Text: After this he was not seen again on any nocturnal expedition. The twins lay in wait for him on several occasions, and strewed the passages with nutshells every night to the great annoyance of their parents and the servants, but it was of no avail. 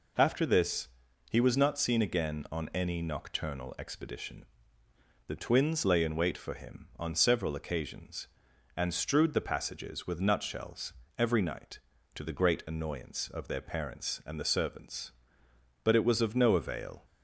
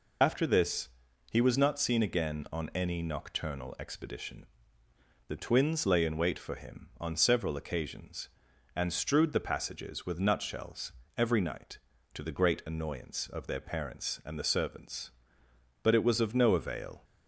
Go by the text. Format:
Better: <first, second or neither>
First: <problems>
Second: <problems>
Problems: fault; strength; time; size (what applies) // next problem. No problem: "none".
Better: first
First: pauses between "this" and "he"; at 0.8 s; 0.42 s long // pauses between "nutshells" and "every"; slight; at 10.9 s; 0.24 s long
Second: loses the start of "After"; at 0.2 s; 45 ms // pauses between "this" and "he"; at 0.8 s; 0.42 s long // pauses between "nutshells" and "every"; slight; at 10.9 s; 0.24 s long